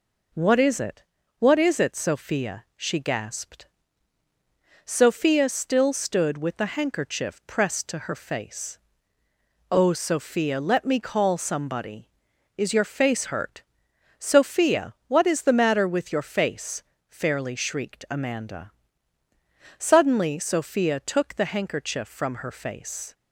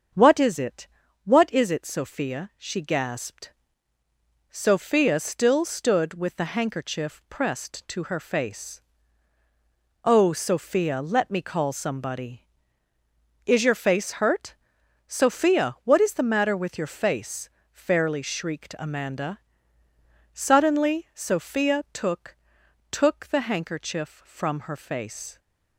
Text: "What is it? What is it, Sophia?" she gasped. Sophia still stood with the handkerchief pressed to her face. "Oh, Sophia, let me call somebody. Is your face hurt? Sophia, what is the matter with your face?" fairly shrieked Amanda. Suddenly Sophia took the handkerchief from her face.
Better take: first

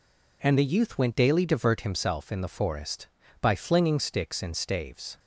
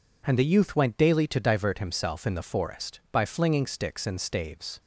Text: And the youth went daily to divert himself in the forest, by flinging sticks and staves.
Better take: second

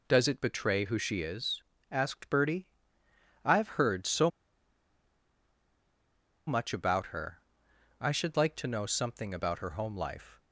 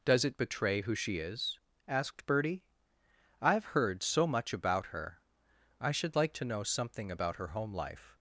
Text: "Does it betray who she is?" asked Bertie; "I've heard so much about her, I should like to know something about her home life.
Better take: second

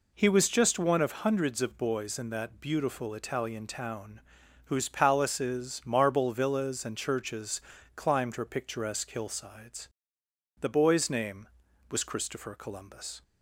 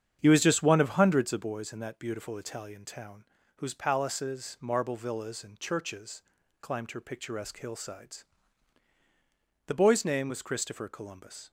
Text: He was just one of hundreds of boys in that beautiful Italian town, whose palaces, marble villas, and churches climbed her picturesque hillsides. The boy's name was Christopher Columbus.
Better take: first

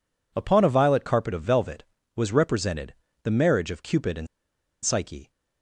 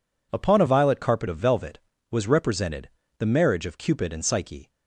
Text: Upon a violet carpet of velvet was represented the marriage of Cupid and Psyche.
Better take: second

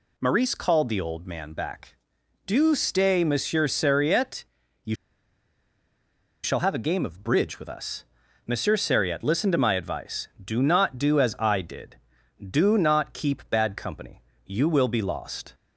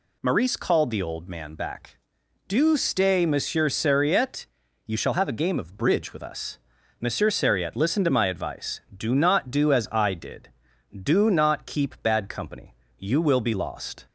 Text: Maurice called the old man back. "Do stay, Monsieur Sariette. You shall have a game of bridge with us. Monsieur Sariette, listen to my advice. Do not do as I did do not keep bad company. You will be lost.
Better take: second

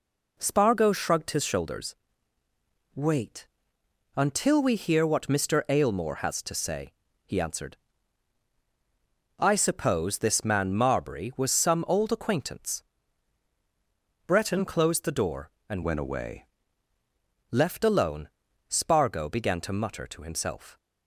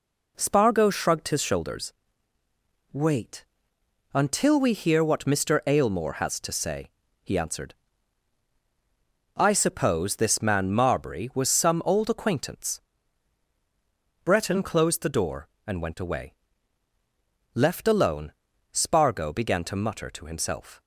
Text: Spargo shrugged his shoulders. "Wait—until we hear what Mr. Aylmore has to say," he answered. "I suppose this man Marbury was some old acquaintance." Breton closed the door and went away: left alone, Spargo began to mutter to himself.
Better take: second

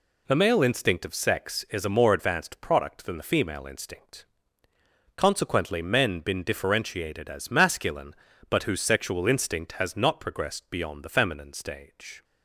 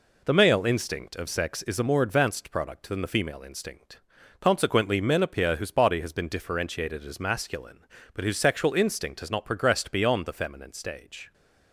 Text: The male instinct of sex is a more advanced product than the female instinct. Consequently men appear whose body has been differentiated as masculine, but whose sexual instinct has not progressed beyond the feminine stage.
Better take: second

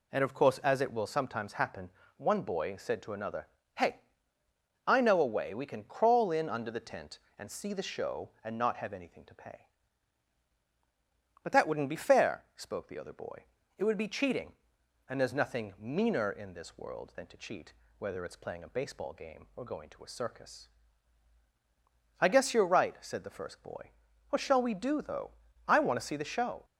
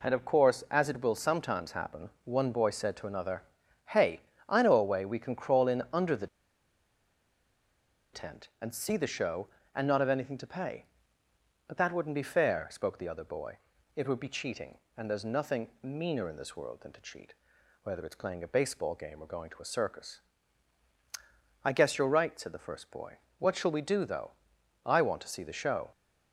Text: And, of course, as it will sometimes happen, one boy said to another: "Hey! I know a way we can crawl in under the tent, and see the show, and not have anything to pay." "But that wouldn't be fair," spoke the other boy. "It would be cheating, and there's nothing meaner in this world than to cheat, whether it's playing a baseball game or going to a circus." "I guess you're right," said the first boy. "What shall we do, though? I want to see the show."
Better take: first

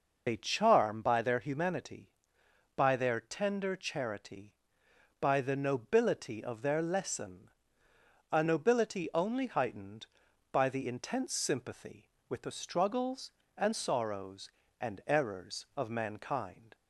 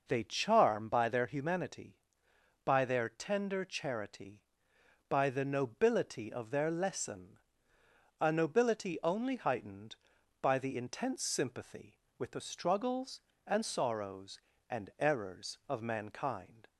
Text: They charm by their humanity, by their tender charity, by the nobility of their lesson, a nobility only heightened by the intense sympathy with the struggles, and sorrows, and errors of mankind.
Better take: second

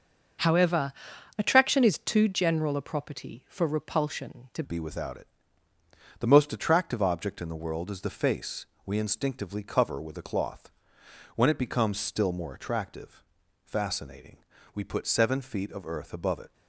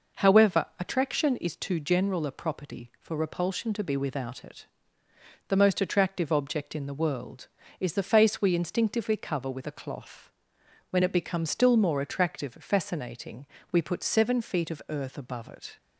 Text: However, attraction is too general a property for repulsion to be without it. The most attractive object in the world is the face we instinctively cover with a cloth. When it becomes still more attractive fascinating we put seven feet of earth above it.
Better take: second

